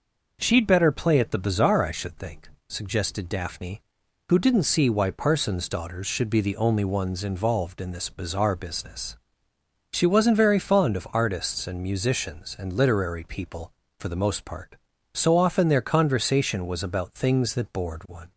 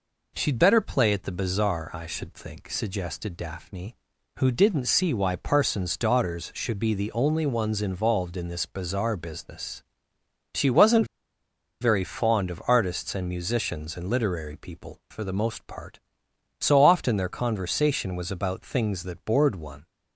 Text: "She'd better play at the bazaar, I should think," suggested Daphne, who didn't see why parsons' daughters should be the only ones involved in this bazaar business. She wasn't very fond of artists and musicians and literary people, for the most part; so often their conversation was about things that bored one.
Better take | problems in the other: first | pauses between "wasn't" and "very"; noticeable; at 11.0 s; 0.75 s long

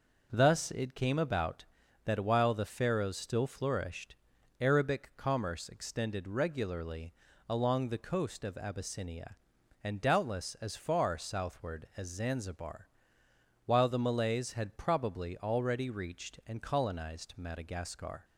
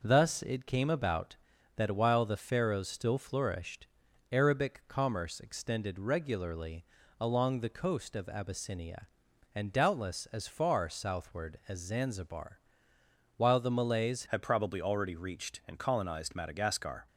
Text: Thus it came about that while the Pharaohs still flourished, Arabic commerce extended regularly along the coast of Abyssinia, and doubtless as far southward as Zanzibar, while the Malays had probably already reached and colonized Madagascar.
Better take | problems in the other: first | pauses between "regularly" and "along"; slight; at 6.8 s; 0.36 s long; slight in the first // changes voice at "had"; from 14.2 s on; 2.8 s long

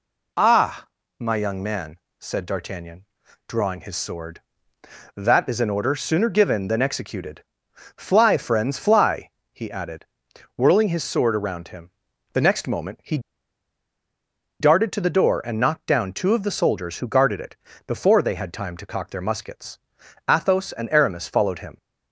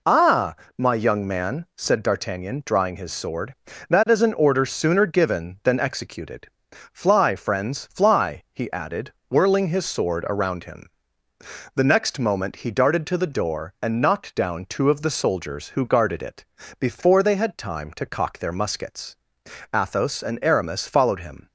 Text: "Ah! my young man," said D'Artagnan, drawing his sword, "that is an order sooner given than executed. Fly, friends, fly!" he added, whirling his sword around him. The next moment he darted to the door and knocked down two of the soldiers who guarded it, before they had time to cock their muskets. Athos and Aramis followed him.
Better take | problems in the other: second | pauses between "he" and "darted"; strong; at 13.1 s; 1.4 s long

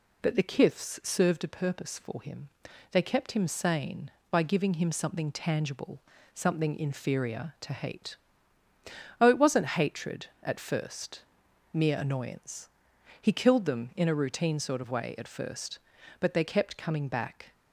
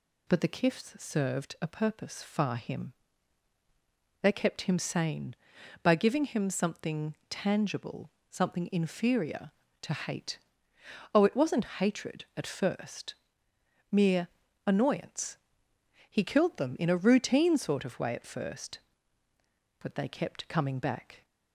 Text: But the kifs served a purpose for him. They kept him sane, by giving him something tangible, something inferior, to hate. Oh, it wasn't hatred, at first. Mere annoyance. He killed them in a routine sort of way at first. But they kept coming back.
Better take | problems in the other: first | says "far" for "for"; at 2.2 s // pauses between "Mere" and "annoyance"; at 14.2 s; 0.38 s long

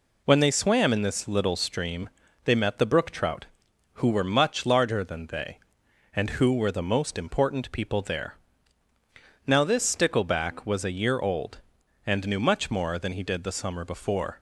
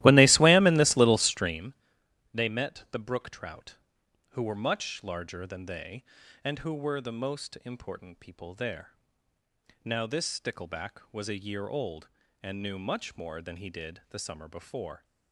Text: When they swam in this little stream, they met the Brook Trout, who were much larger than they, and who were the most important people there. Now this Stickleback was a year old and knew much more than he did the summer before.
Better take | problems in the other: first | starts louder than the rest; strong; until 1.7 s; 16 dB

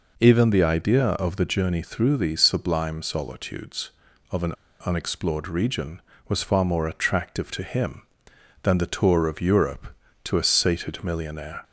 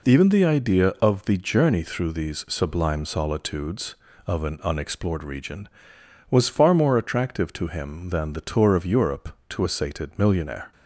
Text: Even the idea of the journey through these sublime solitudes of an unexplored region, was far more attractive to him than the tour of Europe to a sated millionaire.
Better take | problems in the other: second | pauses between "an" and "unexplored"; slight; at 4.5 s; 0.32 s long

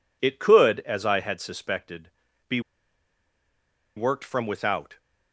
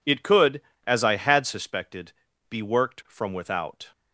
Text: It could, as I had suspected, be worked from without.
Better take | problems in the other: second | pauses between "be" and "worked"; strong; at 2.5 s; 1.3 s long

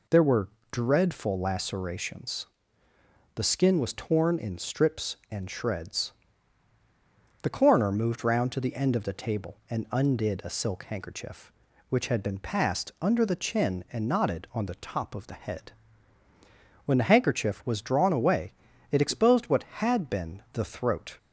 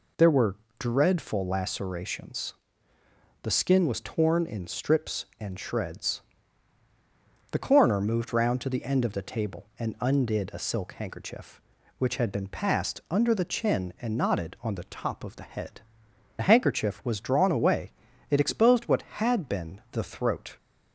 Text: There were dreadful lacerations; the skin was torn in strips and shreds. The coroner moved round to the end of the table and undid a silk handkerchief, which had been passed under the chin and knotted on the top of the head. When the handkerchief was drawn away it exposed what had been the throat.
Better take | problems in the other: first | pauses between "were" and "dreadful"; slight; at 0.5 s; 0.24 s long; slight in the first // skips "When"; at 16.0 s // pauses between "away" and "it"; at 17.9 s; 0.40 s long; also in the first

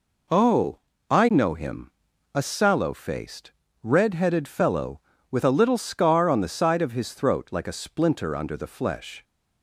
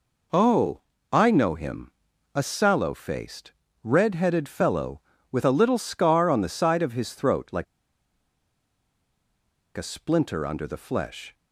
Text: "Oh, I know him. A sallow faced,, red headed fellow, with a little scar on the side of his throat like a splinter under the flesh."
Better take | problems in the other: first | pauses between "like" and "a"; strong; at 7.6 s; 2.1 s long

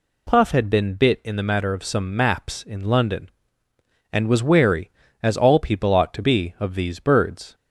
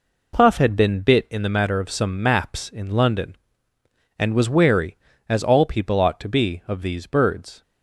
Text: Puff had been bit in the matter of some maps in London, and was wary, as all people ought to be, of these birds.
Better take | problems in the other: first | gets quieter; noticeable; throughout; 6 dB

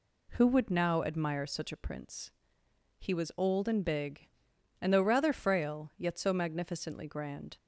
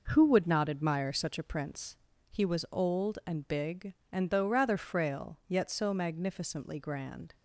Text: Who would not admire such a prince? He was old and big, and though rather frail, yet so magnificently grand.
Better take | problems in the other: second | says "now" for "not"; at 0.7 s

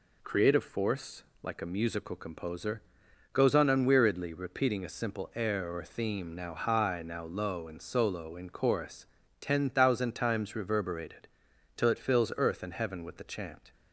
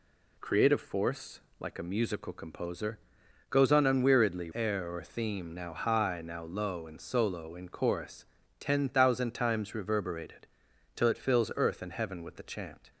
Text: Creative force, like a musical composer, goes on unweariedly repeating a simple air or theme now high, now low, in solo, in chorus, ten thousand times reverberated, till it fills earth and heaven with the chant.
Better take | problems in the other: first | skips "repeating a simple"; at 4.5 s

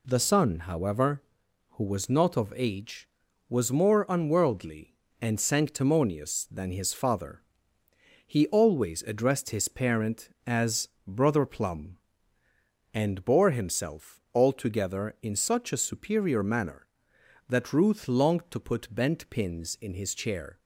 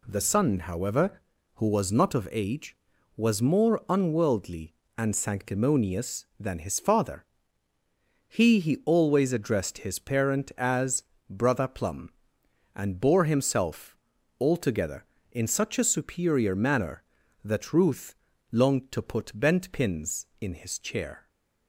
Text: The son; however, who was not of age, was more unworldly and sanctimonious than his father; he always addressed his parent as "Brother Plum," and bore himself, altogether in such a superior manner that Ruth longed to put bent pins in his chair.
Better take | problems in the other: first | says "he" twice; at 8.5 s // pauses between "as" and "Brother"; slight; at 11.0 s; 0.26 s long; slight in the first // pauses between "Ruth" and "longed"; at 18.1 s; 0.38 s long

